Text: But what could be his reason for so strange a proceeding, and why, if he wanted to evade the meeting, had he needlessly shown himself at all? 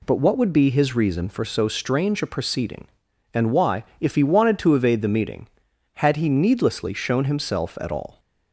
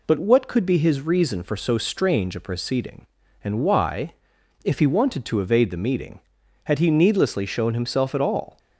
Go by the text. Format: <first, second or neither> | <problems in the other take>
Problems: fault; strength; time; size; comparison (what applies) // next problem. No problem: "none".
second | says "would" for "could"; at 0.3 s